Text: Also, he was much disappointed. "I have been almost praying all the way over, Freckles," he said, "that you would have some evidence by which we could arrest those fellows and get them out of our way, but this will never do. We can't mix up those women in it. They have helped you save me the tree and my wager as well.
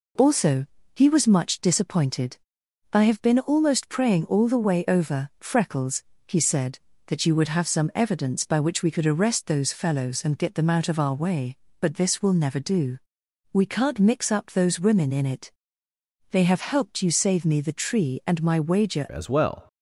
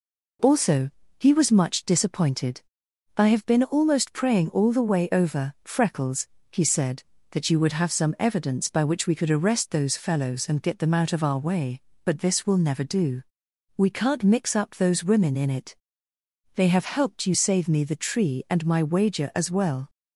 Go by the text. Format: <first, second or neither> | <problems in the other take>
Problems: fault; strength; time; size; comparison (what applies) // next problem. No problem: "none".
second | changes voice at "as"; from 19.0 s on; 0.6 s long